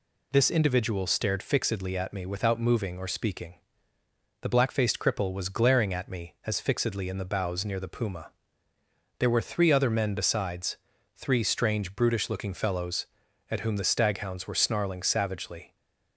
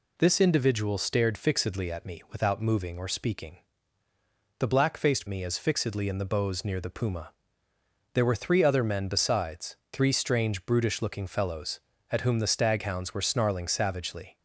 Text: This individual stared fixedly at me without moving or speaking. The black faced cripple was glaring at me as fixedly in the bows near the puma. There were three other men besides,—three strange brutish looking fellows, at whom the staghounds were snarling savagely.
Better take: first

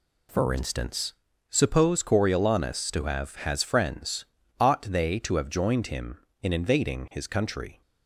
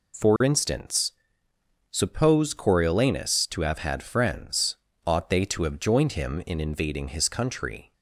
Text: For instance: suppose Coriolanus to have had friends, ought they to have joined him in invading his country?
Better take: second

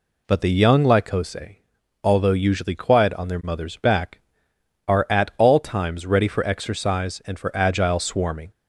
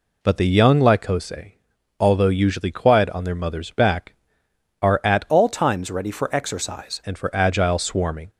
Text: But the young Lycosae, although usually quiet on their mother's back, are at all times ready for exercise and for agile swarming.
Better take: first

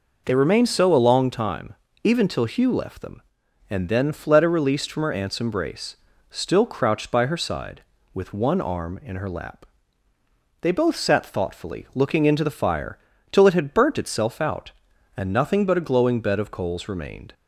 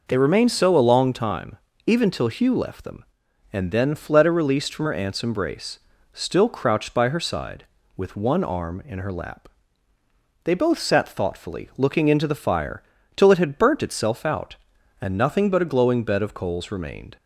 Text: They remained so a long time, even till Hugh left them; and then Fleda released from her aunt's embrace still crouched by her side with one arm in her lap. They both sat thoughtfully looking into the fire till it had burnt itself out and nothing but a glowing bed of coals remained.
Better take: neither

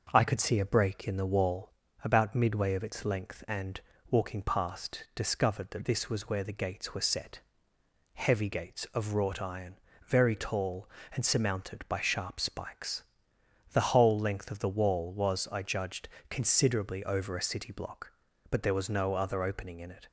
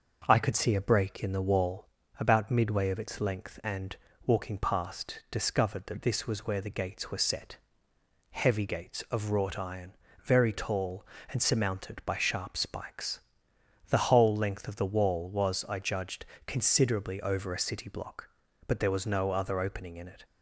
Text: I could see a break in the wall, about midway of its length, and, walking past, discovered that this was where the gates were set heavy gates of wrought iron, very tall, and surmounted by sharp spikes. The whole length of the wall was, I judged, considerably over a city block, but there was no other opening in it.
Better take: neither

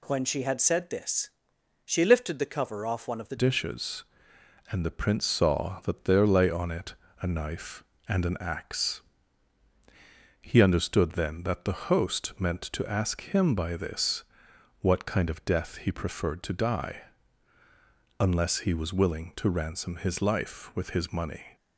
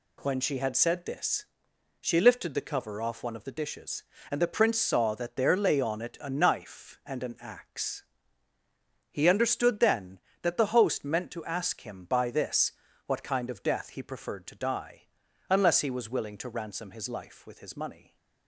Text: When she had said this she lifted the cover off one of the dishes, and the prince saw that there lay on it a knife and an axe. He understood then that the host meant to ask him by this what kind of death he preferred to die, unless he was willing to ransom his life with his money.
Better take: second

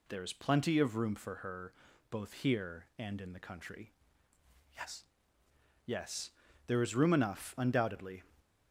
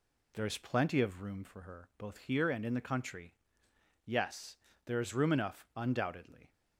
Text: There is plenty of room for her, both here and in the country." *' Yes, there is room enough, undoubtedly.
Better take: second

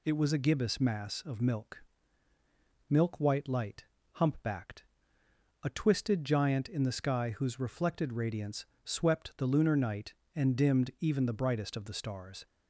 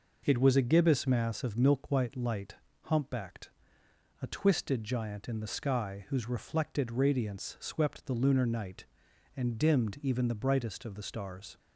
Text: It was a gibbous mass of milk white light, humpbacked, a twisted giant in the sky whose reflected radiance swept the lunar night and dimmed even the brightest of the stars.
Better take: second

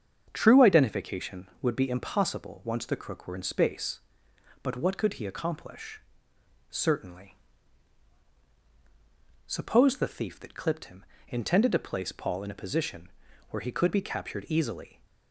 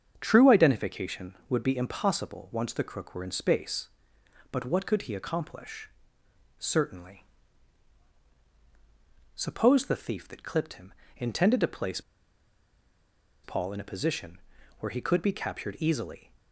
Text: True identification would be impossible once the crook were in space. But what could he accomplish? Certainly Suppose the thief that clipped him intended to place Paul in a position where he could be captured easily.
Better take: first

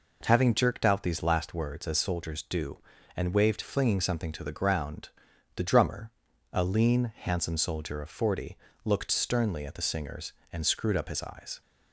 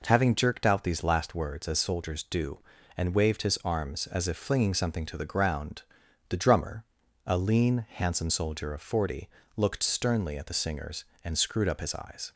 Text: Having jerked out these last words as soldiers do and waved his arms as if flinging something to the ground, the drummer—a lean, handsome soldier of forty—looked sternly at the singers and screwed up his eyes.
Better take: second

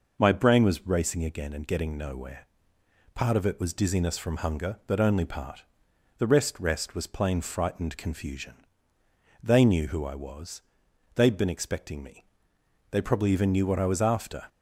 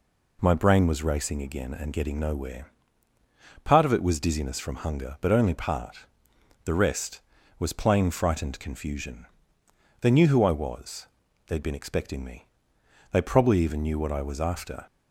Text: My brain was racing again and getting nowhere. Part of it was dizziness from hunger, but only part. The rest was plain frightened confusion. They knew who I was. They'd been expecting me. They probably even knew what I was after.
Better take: second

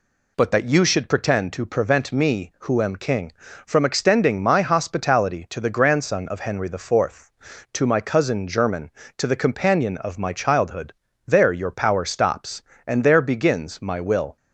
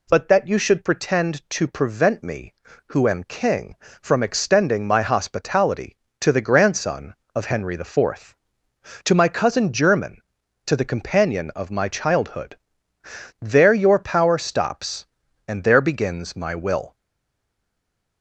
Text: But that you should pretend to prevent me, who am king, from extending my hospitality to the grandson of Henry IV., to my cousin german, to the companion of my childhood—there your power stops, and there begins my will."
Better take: first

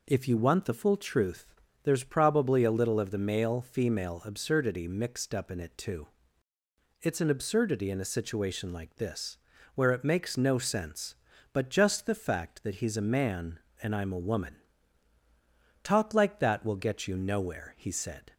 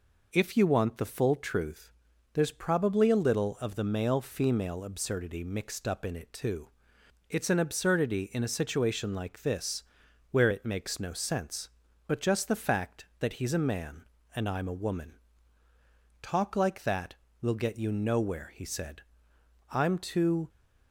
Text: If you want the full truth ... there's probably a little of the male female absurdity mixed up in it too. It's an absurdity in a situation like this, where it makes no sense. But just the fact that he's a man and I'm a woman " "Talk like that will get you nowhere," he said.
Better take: first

